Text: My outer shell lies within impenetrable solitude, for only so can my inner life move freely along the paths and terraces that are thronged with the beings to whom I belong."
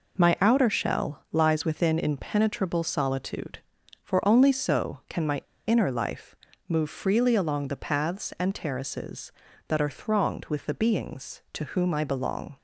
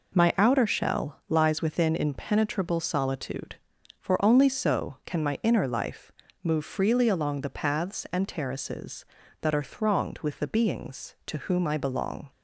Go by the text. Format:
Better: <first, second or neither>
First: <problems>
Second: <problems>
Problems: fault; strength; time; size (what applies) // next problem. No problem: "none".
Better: second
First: pauses between "my" and "inner"; slight; at 5.4 s; 0.23 s long // pauses between "life" and "move"; slight; at 6.3 s; 0.34 s long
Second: pauses between "life" and "move"; slight; at 6.1 s; 0.32 s long